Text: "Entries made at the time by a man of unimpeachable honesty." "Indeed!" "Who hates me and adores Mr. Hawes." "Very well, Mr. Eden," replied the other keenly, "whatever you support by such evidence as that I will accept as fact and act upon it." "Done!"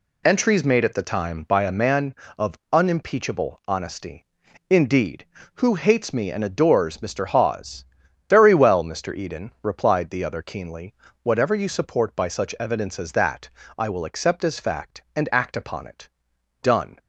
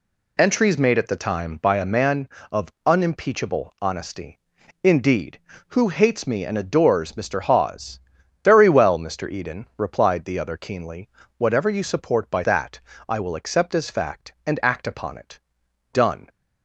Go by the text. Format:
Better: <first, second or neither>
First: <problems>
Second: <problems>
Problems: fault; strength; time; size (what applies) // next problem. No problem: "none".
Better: first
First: pauses between "that" and "I"; slight; at 13.4 s; 0.28 s long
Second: skips "such evidence as"; at 12.4 s // pauses between "that" and "I"; slight; at 12.7 s; 0.28 s long